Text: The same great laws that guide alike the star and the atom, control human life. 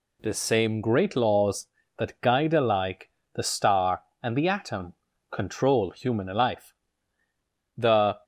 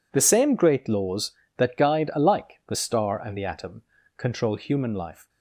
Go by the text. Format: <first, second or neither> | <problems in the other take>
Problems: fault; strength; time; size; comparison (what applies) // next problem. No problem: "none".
second | pauses between "alike" and "the"; slight; at 3.0 s; 0.26 s long // goes on to say "The"; slight; from 7.7 s on; 0.42 s long